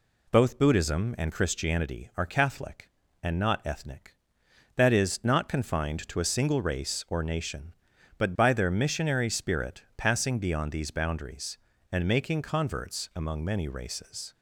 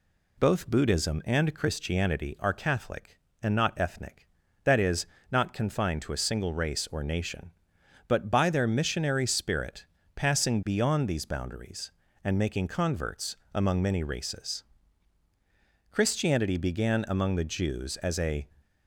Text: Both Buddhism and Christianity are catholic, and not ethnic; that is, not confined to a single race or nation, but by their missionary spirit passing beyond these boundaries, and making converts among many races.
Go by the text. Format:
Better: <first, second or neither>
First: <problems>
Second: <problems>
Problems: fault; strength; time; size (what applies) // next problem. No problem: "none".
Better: first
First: none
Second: pauses between "spirit" and "passing"; slight; at 9.8 s; 0.30 s long // pauses between "converts" and "among"; slight; at 13.3 s; 0.16 s long // goes on to say "Christianity began among the Jews as a"; strong; from 15.9 s on; 2.5 s long